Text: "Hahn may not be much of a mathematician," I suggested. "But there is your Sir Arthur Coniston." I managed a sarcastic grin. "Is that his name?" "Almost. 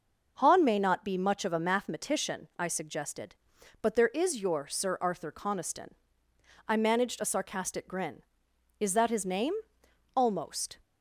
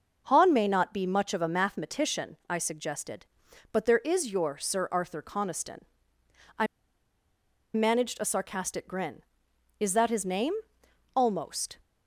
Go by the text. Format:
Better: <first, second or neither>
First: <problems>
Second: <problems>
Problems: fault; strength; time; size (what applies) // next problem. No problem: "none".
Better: first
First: none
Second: pauses between "I" and "managed"; at 6.6 s; 1.0 s long